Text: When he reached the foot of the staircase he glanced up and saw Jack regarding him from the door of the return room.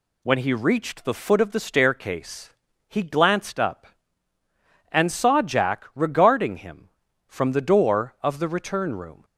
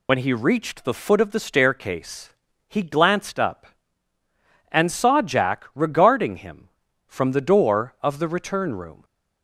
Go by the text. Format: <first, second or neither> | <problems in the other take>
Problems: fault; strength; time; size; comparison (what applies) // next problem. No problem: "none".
first | loses the start of "When"; at 0.0 s; 55 ms // pauses between "staircase" and "he"; at 2.2 s; 0.38 s long; also in the first